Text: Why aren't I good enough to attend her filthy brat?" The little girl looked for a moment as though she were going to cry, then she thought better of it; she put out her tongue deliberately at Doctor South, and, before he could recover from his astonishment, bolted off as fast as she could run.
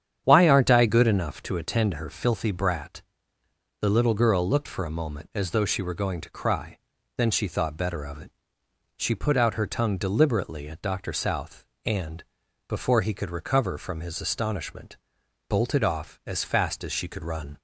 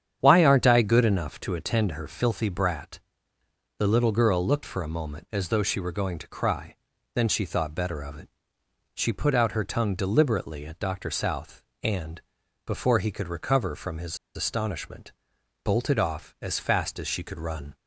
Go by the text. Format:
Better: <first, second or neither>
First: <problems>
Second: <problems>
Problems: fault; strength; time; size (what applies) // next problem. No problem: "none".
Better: first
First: starts louder than the rest; strong; until 1.2 s; 9 dB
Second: starts louder than the rest; strong; until 1.2 s; 9 dB // pauses between "his" and "astonishment"; slight; at 14.1 s; 0.19 s long